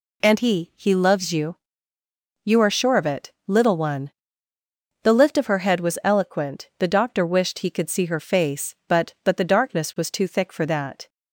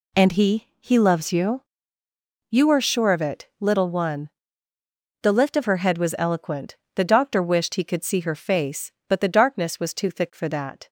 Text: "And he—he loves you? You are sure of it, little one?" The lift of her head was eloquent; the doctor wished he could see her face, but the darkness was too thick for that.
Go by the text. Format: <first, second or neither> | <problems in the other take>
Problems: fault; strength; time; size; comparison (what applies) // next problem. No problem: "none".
second | says "but" twice; at 9.2 s